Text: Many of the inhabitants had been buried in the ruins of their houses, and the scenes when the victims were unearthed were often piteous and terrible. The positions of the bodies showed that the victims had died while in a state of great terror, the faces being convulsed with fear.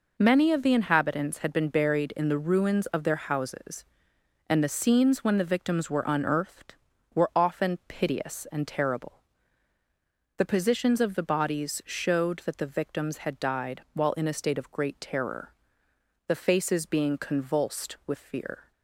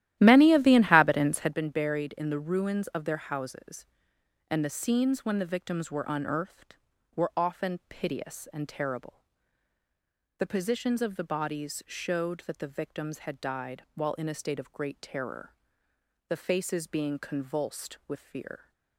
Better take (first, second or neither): first